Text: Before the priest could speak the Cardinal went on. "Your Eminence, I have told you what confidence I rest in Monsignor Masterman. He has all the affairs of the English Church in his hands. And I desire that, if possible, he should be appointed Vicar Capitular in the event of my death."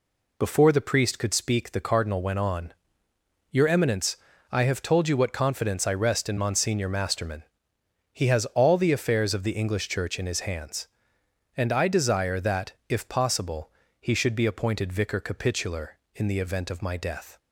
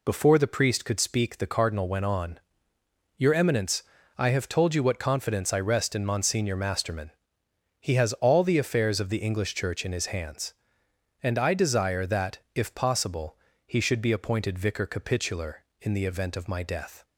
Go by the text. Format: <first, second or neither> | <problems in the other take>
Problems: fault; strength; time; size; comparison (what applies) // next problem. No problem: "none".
neither | none